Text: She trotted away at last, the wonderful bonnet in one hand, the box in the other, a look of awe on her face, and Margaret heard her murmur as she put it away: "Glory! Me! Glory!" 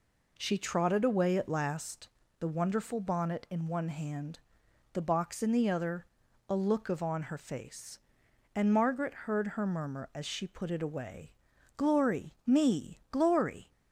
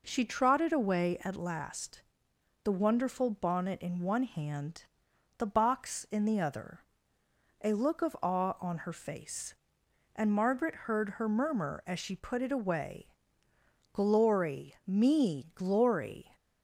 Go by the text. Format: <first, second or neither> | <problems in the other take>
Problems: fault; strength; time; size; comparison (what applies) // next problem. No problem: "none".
second | skips "awe"; at 7.0 s